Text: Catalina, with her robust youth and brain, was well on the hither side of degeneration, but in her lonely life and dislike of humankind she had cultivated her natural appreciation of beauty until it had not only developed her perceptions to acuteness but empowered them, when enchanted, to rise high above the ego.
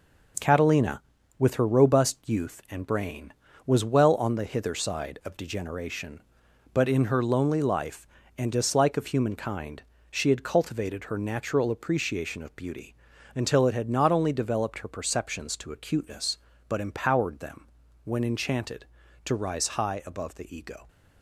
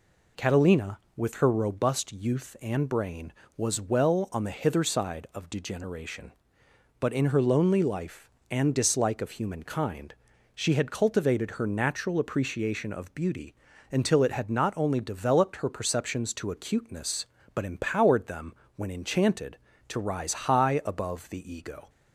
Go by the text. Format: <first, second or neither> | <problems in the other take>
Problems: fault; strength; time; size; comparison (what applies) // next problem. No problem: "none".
second | gets quieter; strong; throughout; 7 dB // pauses between "humankind" and "she"; slight; at 9.8 s; 0.30 s long; also in the second // pauses between "beauty" and "until"; at 12.9 s; 0.40 s long; slight in the second